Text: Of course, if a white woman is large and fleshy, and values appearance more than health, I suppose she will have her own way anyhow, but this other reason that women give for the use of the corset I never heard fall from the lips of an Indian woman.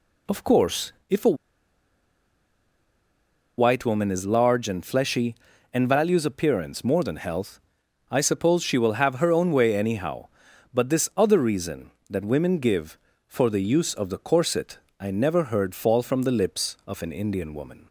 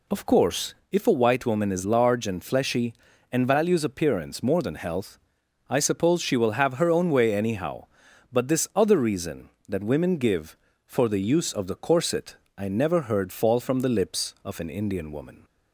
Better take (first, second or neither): second